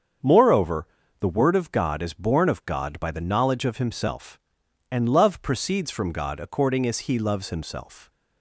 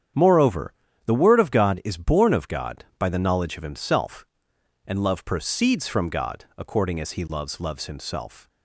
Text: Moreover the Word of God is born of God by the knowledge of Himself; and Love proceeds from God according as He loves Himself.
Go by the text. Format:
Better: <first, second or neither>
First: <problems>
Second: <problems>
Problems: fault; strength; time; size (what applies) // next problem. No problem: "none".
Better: first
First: starts louder than the rest; strong; until 1.5 s; 7 dB // pauses between "Moreover" and "the"; slight; at 0.8 s; 0.34 s long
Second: starts louder than the rest; strong; until 1.4 s; 9 dB // pauses between "Moreover" and "the"; slight; at 0.7 s; 0.34 s long // says "loves" twice; at 7.6 s